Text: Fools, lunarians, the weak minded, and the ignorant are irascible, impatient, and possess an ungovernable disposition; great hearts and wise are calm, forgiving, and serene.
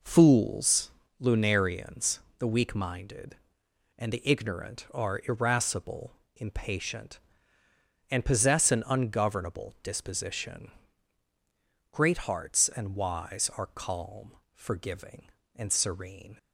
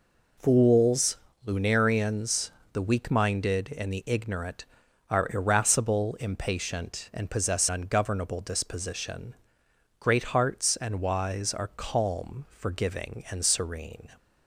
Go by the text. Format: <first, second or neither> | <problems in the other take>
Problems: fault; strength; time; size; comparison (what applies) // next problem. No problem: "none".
first | skips "an"; at 7.7 s